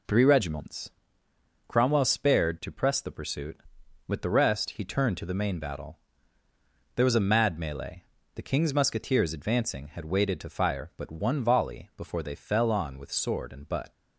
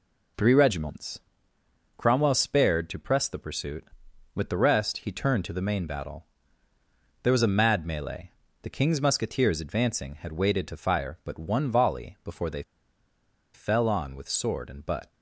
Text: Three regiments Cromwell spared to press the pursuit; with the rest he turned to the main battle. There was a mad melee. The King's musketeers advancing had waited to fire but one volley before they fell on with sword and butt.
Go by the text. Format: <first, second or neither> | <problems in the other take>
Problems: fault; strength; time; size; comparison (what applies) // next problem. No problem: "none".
first | pauses between "regiments" and "Cromwell"; noticeable; at 1.2 s; 0.76 s long; noticeable in the first // pauses between "they" and "fell"; noticeable; at 12.6 s; 0.91 s long